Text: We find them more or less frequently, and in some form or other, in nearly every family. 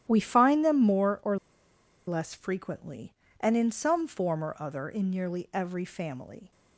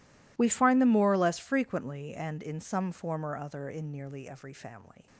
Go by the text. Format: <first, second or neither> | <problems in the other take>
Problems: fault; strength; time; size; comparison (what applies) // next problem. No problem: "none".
second | starts louder than the rest; strong; until 1.0 s; 11.5 dB // pauses between "or" and "less"; noticeable; at 1.3 s; 0.71 s long